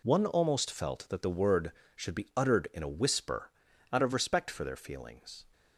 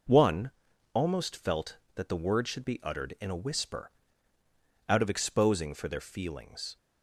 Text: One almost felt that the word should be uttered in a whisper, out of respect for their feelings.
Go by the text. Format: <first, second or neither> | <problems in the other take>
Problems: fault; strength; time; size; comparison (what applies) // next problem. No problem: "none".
first | pauses between "One" and "almost"; at 0.5 s; 0.40 s long // says "exposing" for "respect"; at 5.1 s